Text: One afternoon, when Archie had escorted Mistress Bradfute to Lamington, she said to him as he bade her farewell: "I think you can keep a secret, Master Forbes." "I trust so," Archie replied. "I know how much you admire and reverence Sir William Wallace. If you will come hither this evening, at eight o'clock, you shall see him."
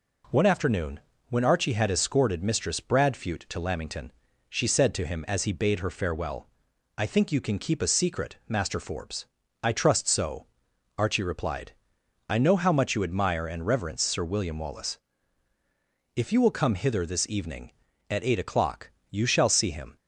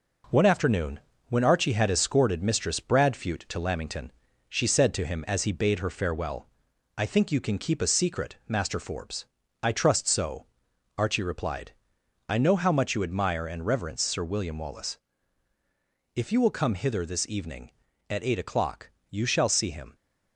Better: first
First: none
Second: gets quieter; noticeable; throughout; 4 dB

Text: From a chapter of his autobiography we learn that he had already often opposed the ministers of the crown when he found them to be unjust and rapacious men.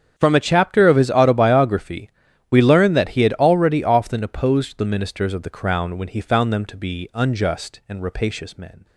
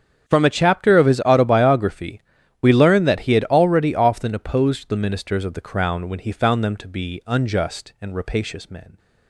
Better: neither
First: starts louder than the rest; strong; until 1.1 s; 7.5 dB // pauses between "autobiography" and "we"; at 2.0 s; 0.40 s long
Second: starts louder than the rest; strong; until 1.3 s; 8 dB // pauses between "autobiography" and "we"; at 2.1 s; 0.40 s long

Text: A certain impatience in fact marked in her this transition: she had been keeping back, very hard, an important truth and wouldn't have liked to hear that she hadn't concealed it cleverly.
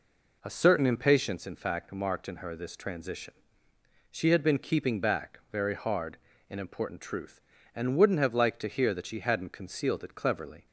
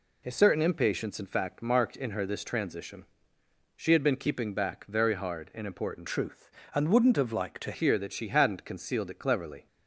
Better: first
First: none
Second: changes voice from "truth" to "to"; from 6.0 to 7.7 s; 1.7 s long

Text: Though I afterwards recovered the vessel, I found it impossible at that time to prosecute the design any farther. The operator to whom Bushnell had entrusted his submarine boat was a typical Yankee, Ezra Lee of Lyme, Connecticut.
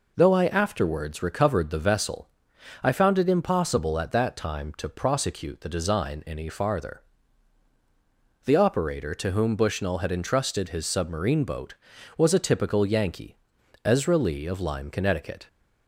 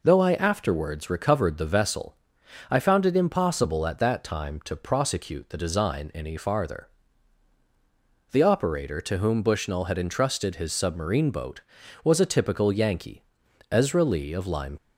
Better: first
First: none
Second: stops before "Connecticut"; at 14.7 s

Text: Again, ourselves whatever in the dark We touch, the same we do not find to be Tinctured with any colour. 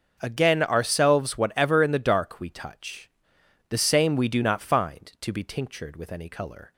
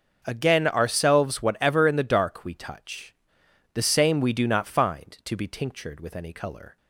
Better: neither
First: starts louder than the rest; noticeable; until 1.2 s; 6 dB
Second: starts louder than the rest; noticeable; until 1.2 s; 6 dB

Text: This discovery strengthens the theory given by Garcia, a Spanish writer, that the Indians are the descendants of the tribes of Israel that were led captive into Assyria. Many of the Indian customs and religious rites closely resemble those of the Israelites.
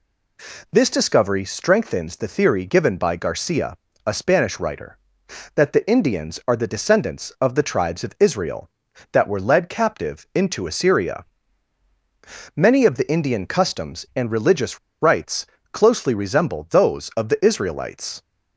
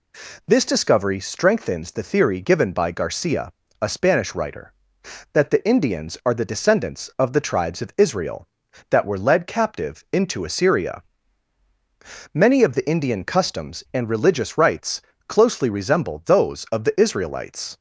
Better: second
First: pauses between "religious" and "rites"; slight; at 14.7 s; 0.24 s long // pauses between "rites" and "closely"; slight; at 15.4 s; 0.28 s long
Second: pauses between "rites" and "closely"; slight; at 15.0 s; 0.28 s long

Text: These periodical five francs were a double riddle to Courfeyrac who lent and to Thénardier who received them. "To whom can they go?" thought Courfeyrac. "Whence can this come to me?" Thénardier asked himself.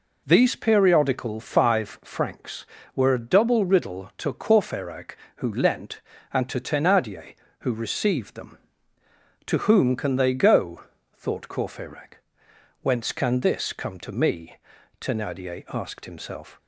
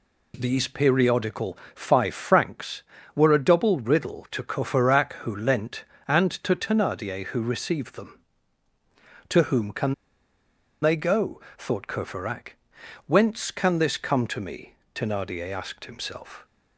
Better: first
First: none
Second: pauses between "periodical" and "five"; slight; at 1.5 s; 0.18 s long // pauses between "can" and "they"; noticeable; at 9.9 s; 0.88 s long

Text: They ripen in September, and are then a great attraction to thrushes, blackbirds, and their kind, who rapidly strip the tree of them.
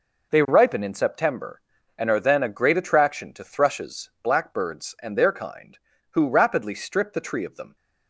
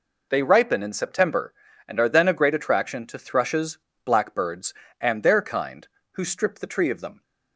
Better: first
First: none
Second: skips "rapidly"; at 6.2 s

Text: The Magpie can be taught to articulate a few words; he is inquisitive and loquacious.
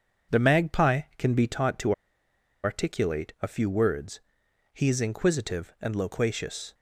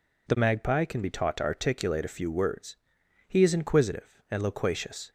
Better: second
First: pauses between "to" and "articulate"; noticeable; at 1.9 s; 0.71 s long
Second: none

